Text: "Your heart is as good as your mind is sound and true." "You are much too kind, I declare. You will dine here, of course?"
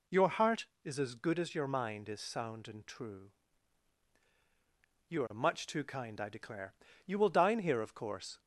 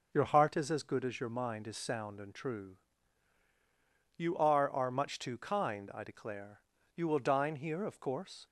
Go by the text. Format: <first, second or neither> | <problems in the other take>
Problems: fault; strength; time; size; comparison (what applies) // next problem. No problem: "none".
first | says "are" twice; at 4.6 s